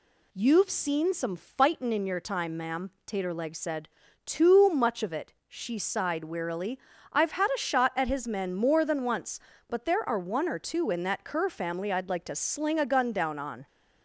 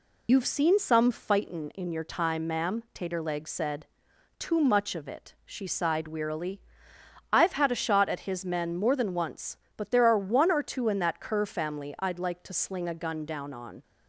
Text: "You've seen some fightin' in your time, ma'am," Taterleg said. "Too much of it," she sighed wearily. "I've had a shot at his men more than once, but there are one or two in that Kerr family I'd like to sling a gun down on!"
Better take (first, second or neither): first